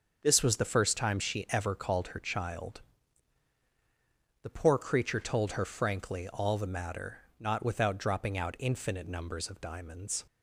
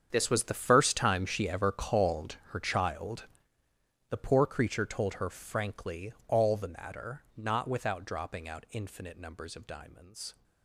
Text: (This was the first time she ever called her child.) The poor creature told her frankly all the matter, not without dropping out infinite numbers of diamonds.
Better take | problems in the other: first | gets quieter; strong; throughout; 15.5 dB // starts louder than the rest; strong; until 1.1 s; 7.5 dB; also in the first // pauses between "frankly" and "all"; slight; at 6.1 s; 0.16 s long

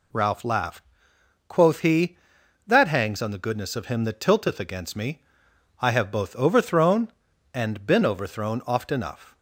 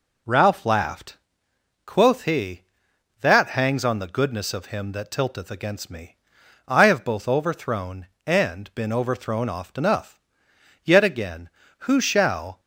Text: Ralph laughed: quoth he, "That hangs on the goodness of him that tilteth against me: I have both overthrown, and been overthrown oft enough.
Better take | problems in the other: first | goes on to say "Yet again who shall"; strong; from 10.8 s on; 1.7 s long

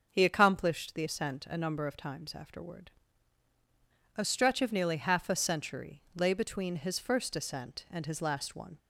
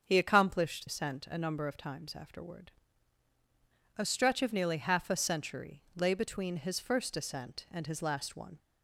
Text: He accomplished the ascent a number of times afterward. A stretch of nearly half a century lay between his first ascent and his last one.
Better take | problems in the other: first | starts louder than the rest; until 1.0 s; 7 dB // skips "the"; at 0.8 s

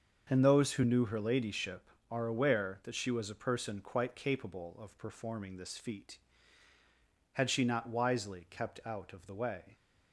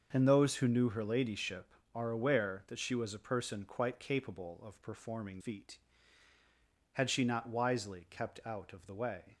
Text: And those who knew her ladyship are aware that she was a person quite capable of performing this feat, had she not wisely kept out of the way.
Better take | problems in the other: first | starts louder than the rest; until 1.1 s; 6.5 dB; also in the first // skips "this"; at 5.3 s

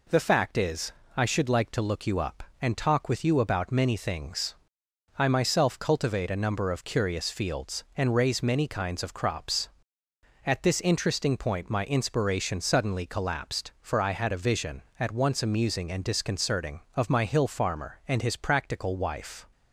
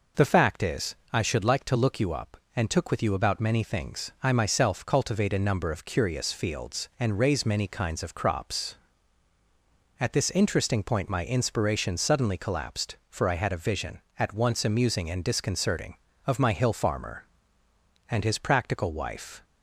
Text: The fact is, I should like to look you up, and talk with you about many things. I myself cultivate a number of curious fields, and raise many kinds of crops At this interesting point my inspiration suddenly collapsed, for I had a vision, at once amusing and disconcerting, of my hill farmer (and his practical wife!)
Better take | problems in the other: first | says "took" for "talk"; at 2.6 s

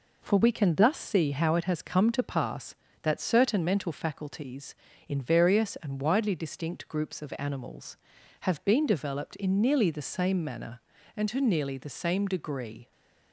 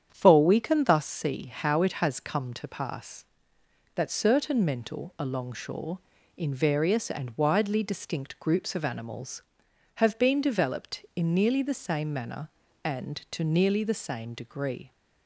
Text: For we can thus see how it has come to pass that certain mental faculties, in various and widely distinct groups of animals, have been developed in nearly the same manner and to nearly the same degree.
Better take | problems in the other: first | starts louder than the rest; strong; until 1.1 s; 8.5 dB // says "alongshore" for "faculties"; at 5.1 s

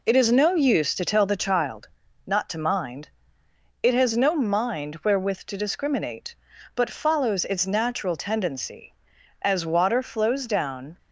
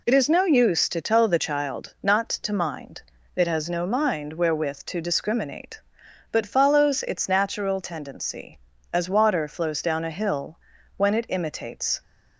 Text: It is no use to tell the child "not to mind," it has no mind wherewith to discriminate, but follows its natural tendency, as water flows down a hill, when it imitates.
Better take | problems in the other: second | pauses between "child" and "not"; at 1.8 s; 0.38 s long // stops before "a hill when it imitates"; at 10.9 s

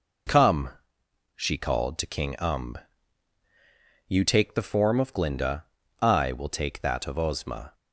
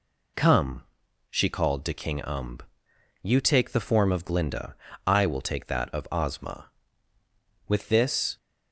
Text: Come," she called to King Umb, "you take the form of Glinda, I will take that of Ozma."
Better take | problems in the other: first | goes on to say "With this"; noticeable; from 7.6 s on; 0.70 s long

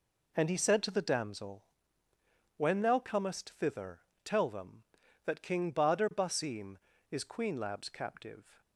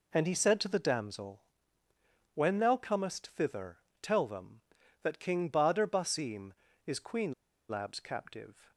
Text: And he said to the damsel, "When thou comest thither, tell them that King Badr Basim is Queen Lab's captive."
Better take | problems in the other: first | pauses between "Queen" and "Lab's"; at 7.3 s; 0.37 s long

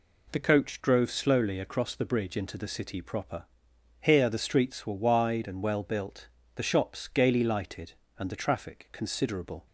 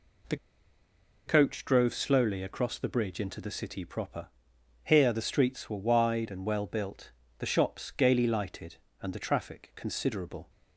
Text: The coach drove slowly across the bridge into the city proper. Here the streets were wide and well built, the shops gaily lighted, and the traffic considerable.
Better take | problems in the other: first | pauses between "The" and "coach"; noticeable; at 0.3 s; 0.90 s long

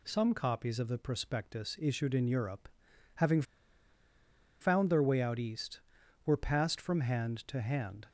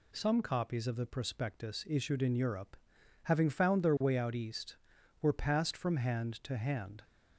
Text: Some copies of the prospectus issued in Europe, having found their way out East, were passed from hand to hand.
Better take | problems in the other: second | pauses between "having" and "found"; at 3.4 s; 1.1 s long

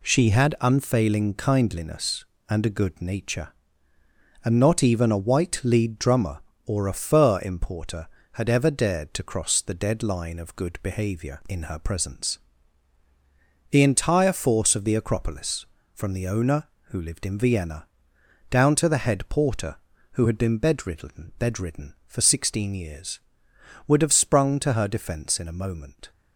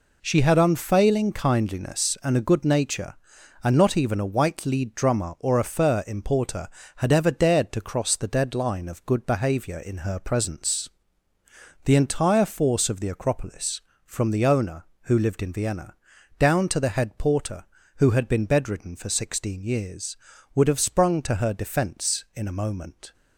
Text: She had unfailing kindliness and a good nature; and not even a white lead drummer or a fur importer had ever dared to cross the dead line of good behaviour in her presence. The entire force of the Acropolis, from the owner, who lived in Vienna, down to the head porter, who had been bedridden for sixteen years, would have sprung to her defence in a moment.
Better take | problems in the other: second | says "bedridden" twice; at 21.3 s

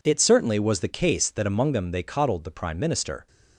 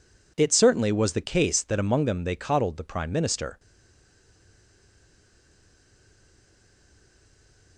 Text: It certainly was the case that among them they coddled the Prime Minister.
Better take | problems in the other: first | stays silent after the last word; strong; from 3.5 s on; 4.2 s long

